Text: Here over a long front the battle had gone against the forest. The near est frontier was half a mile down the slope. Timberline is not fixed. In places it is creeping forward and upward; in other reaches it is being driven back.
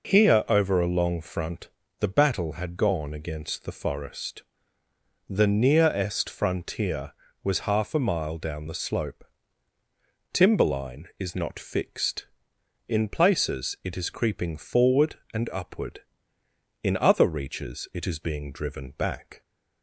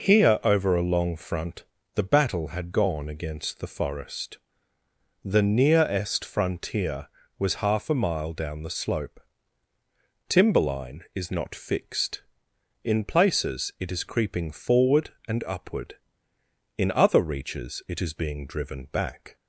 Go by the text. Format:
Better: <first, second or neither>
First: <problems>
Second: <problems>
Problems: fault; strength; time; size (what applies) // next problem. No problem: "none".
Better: neither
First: pauses between "front" and "the"; slight; at 1.6 s; 0.30 s long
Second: pauses between "front" and "the"; slight; at 1.6 s; 0.30 s long